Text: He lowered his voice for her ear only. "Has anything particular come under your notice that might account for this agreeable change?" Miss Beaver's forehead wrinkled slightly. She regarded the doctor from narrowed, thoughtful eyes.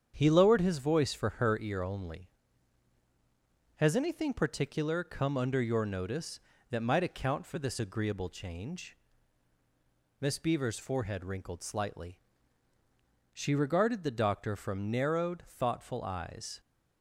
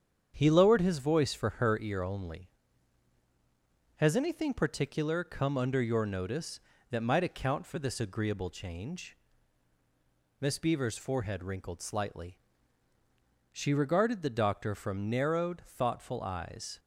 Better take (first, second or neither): neither